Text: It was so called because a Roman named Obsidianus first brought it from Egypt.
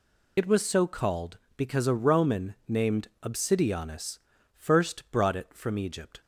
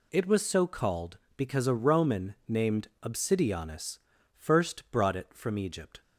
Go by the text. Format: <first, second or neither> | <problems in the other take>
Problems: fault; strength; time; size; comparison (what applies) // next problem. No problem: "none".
second | loses the start of "It"; at 0.3 s; 60 ms // pauses between "named" and "Obsidianus"; slight; at 3.0 s; 0.16 s long; slight in the second // pauses between "Obsidianus" and "first"; at 4.1 s; 0.38 s long; also in the second